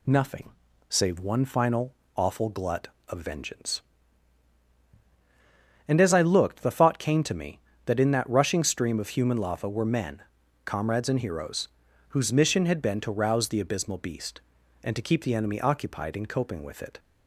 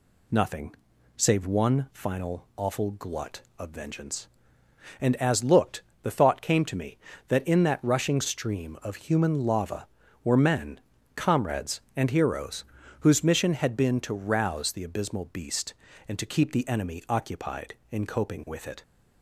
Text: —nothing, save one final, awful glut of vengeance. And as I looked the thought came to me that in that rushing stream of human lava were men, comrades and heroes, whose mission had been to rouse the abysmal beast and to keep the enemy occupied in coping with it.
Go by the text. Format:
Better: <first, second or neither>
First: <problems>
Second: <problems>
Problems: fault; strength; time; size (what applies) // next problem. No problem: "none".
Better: first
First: none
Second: skips "I"; at 5.4 s // pauses between "looked" and "the"; slight; at 5.8 s; 0.20 s long